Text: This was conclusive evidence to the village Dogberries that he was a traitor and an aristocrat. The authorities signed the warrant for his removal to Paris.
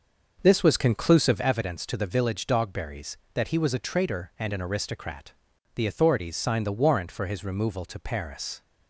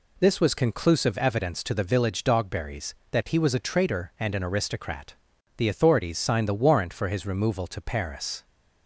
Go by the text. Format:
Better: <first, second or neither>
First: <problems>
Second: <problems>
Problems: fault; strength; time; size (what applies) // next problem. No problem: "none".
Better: second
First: starts louder than the rest; noticeable; until 1.6 s; 6 dB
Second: none